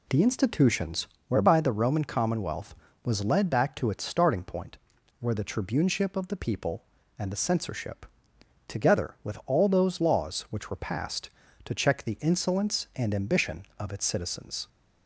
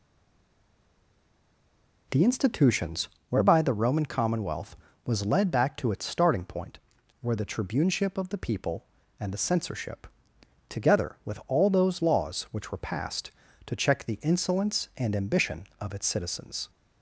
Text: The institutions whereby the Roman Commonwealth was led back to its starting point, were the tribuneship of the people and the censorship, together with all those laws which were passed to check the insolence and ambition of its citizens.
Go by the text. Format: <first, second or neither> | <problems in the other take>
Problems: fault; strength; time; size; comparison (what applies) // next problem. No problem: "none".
first | stays silent before the first word; noticeable; until 2.1 s; 2.1 s long // pauses between "institutions" and "whereby"; slight; at 3.0 s; 0.22 s long; slight in the first